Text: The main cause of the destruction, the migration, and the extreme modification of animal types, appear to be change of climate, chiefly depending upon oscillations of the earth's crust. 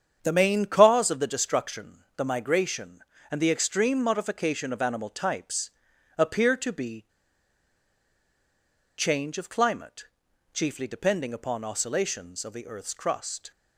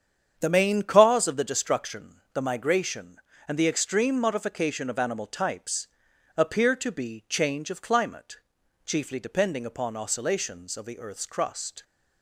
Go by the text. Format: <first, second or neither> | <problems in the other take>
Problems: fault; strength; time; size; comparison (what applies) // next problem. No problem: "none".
second | starts louder than the rest; strong; until 1.2 s; 8 dB; strong in the second // pauses between "be" and "change"; strong; at 7.0 s; 1.9 s long